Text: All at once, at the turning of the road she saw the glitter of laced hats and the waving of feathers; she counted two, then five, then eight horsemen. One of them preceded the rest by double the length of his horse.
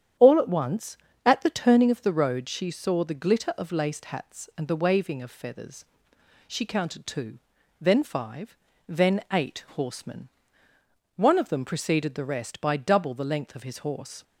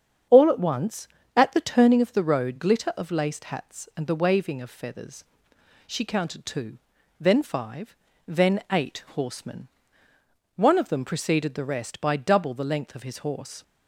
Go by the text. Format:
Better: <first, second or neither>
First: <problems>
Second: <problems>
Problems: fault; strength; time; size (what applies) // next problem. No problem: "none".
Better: first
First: starts louder than the rest; strong; until 1.4 s; 9.5 dB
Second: starts louder than the rest; strong; until 1.5 s; 8 dB // skips "she saw the"; at 2.5 s